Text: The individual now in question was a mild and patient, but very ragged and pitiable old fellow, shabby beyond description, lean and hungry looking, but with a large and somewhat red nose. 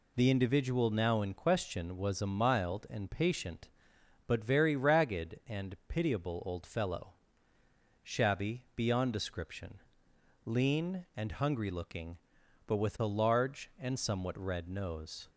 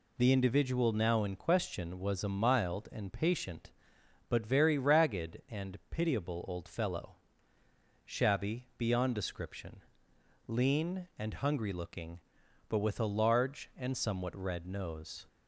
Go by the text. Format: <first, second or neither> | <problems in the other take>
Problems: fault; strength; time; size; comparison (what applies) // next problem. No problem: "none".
neither | none